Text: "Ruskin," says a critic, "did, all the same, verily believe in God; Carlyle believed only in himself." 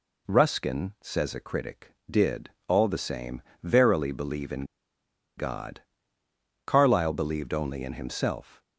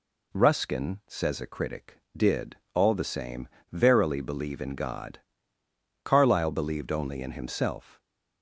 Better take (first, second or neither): second